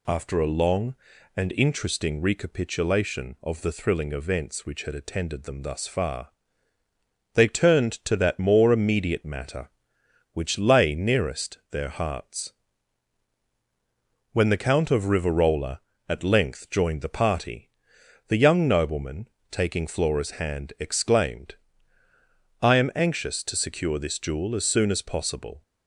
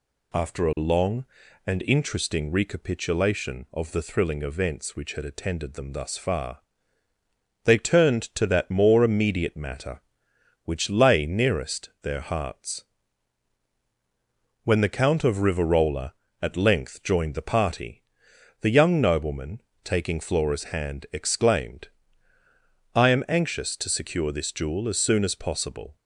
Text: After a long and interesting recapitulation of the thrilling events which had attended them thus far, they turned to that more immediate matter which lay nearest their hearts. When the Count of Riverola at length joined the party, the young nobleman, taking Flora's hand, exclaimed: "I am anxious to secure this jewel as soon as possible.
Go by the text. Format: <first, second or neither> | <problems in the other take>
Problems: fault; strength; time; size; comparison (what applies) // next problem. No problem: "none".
neither | none